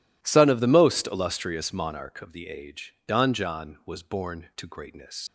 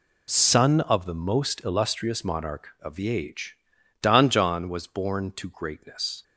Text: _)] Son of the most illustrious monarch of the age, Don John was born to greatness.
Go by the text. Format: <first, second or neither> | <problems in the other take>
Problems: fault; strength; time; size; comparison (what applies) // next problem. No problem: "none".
second | leaves "greatness" unfinished; at 5.2 s; 65 ms